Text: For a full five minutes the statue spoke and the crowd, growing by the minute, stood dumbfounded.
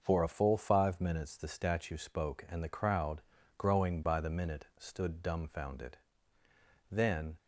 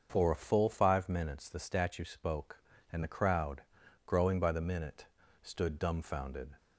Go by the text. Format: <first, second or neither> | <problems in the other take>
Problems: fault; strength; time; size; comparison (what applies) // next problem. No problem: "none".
second | starts louder than the rest; noticeable; until 1.0 s; 6 dB; also in the second // goes on to say "Then"; slight; from 6.9 s on; 0.46 s long